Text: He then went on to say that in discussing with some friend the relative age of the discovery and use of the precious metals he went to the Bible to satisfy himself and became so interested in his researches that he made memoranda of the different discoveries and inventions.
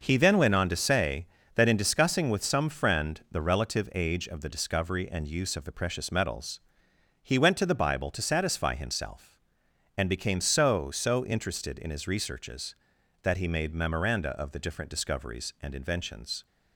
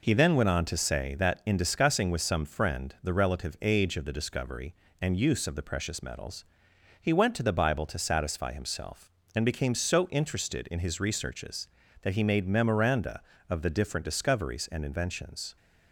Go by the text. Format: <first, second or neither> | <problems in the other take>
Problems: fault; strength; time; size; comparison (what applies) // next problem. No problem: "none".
second | pauses between "metals" and "he"; noticeable; at 6.5 s; 0.62 s long; noticeable in the second // says "so" twice; at 10.8 s